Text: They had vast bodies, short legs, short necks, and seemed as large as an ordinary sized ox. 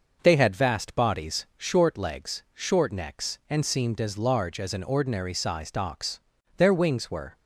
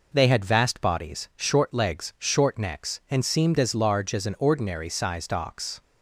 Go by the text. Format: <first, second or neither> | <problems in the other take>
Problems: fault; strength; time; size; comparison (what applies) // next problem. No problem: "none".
second | goes on to say "Their wings were"; noticeable; from 6.5 s on; 0.80 s long